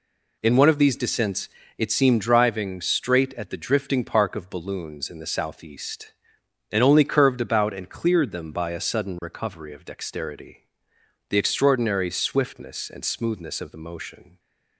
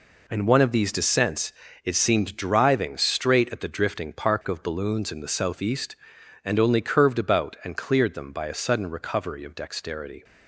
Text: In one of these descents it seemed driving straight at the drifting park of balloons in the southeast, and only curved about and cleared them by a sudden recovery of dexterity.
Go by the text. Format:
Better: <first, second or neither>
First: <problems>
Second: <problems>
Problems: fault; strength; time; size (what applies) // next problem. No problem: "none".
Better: second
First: pauses between "descents" and "it"; slight; at 1.4 s; 0.30 s long // goes on to say "The extraordinary swiftness and smoothness of the motion"; strong; from 11.2 s on; 3.1 s long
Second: pauses between "descents" and "it"; slight; at 1.5 s; 0.32 s long